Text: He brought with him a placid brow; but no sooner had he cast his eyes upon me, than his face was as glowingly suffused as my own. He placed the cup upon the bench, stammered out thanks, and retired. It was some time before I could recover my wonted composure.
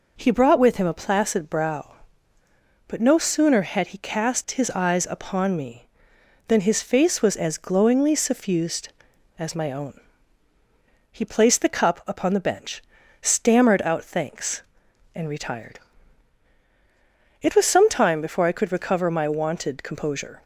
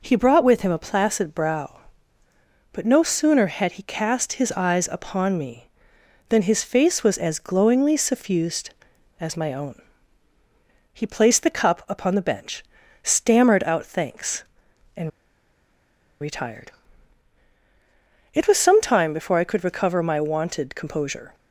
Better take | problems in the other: first | pauses between "and" and "retired"; at 15.0 s; 1.1 s long

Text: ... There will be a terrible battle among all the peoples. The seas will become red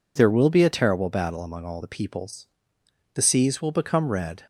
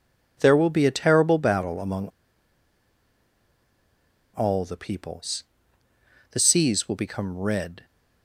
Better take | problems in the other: first | pauses between "among" and "all"; strong; at 2.0 s; 2.2 s long

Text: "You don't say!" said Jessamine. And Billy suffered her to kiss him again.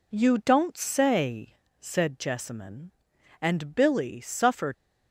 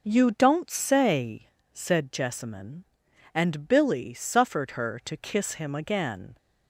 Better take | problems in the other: second | stops before "her to kiss him again"; at 4.7 s

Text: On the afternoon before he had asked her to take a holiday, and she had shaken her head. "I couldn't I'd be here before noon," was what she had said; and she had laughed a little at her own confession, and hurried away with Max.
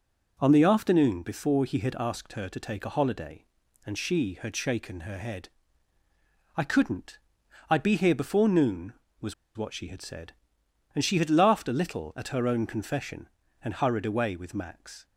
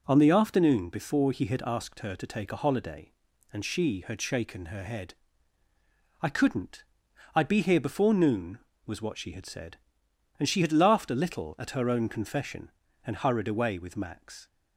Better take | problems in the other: second | pauses between "couldn't" and "I'd"; noticeable; at 7.1 s; 0.50 s long; noticeable in the second // pauses between "was" and "what"; slight; at 9.3 s; 0.22 s long

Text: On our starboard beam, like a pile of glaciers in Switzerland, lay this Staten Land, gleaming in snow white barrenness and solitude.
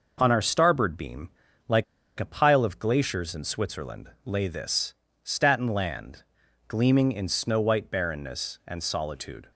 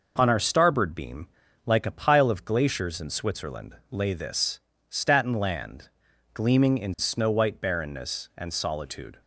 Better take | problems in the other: second | pauses between "like" and "a"; slight; at 1.8 s; 0.34 s long // pauses between "this" and "Staten"; slight; at 4.9 s; 0.30 s long; slight in the second

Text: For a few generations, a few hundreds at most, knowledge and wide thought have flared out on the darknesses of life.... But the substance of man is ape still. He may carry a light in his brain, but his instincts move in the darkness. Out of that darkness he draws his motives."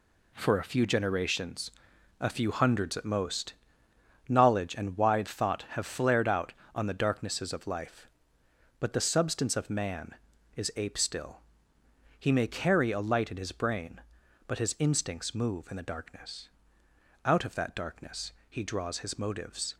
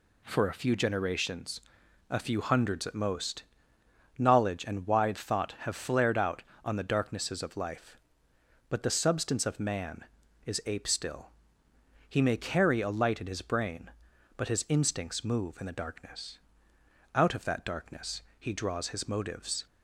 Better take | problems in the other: second | gets quieter; strong; throughout; 8 dB // pauses between "darkness" and "he"; slight; at 18.3 s; 0.18 s long; slight in the second

